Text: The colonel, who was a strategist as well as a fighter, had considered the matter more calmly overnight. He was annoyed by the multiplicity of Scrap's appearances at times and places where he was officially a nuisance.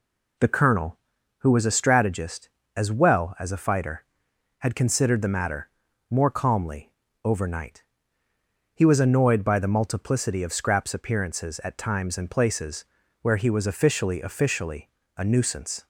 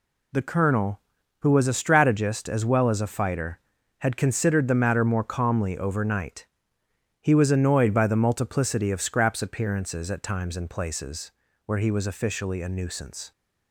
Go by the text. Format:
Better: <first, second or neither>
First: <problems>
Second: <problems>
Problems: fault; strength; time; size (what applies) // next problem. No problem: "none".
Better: second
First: pauses between "matter" and "more"; at 5.6 s; 0.42 s long // pauses between "calmly" and "overnight"; slight; at 6.9 s; 0.34 s long // pauses between "places" and "where"; at 12.8 s; 0.38 s long // says "officially" twice; at 14.2 s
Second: pauses between "places" and "where"; slight; at 11.3 s; 0.34 s long